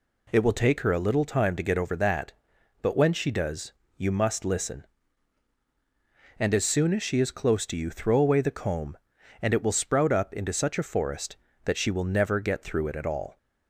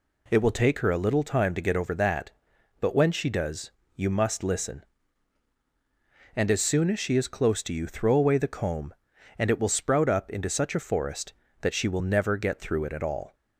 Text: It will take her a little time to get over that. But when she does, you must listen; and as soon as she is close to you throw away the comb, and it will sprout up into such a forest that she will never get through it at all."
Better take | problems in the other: neither | none

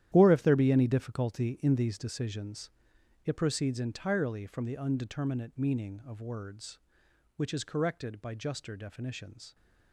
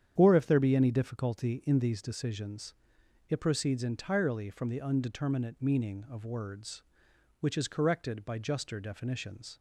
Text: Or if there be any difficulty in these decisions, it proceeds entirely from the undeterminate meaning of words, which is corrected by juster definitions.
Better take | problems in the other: second | gets quieter; strong; throughout; 12.5 dB // starts louder than the rest; strong; until 1.1 s; 11.5 dB; strong in the second

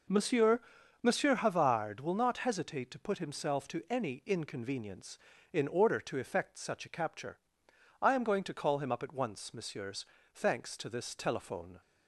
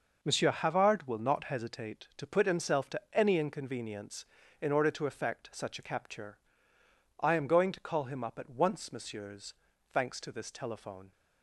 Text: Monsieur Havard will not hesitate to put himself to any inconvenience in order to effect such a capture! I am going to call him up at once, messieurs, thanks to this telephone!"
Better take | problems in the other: second | says "Monsieur" twice; at 1.0 s

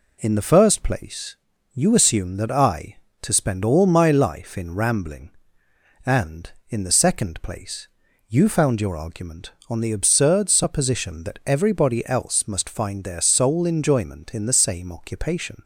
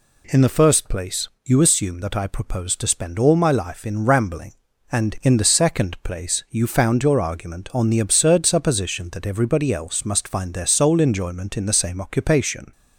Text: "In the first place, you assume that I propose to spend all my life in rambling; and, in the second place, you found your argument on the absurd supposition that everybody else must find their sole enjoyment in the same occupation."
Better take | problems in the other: second | skips "propose"; at 3.0 s

